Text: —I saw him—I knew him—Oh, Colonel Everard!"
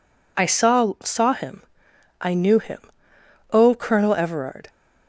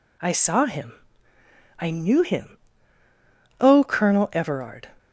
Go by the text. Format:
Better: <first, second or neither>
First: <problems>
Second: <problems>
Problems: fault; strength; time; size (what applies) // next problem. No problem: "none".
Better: second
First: says "saw" twice; at 1.0 s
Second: none